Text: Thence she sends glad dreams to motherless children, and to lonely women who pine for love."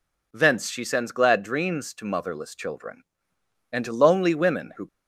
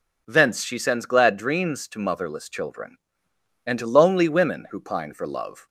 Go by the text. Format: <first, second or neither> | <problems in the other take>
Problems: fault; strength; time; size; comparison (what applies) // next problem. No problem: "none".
second | stops before "pine for love"; at 4.8 s